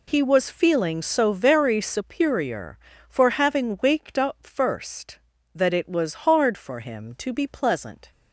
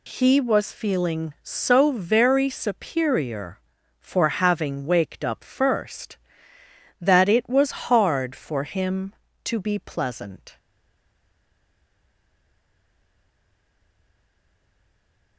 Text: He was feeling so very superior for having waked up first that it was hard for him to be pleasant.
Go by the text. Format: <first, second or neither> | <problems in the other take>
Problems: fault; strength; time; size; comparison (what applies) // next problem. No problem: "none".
first | stays silent after the last word; strong; from 10.5 s on; 4.8 s long